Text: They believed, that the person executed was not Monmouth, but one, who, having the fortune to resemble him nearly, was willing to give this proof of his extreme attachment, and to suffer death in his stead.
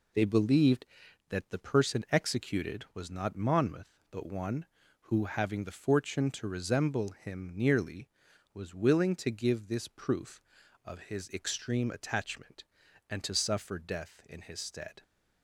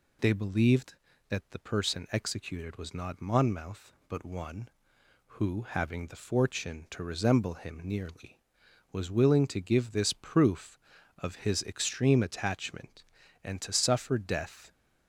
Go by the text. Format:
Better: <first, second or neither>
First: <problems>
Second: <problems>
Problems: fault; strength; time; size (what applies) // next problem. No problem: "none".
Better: first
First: none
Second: stops before "in his stead"; at 14.7 s